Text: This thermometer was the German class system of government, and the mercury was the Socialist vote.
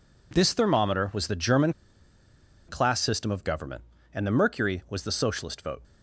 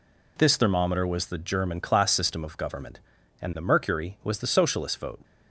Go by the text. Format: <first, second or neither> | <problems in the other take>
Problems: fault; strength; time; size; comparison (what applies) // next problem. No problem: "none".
second | pauses between "German" and "class"; noticeable; at 1.7 s; 0.95 s long